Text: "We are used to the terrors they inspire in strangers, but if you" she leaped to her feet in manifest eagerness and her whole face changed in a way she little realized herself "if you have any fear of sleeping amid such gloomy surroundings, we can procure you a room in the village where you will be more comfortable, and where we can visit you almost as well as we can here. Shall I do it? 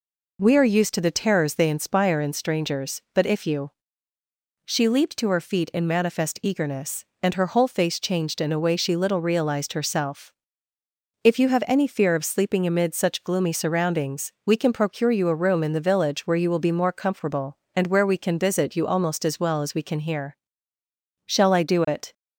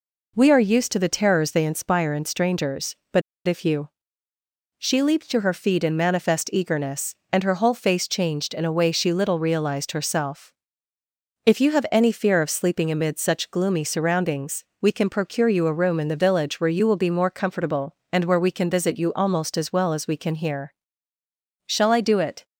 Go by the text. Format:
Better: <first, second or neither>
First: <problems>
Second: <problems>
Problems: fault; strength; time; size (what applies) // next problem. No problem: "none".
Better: first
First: pauses between "you" and "she"; noticeable; at 3.7 s; 0.92 s long // pauses between "herself" and "if"; noticeable; at 10.3 s; 0.90 s long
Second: pauses between "but" and "if"; slight; at 3.2 s; 0.25 s long // pauses between "you" and "she"; noticeable; at 3.8 s; 0.90 s long // pauses between "herself" and "if"; noticeable; at 10.5 s; 0.94 s long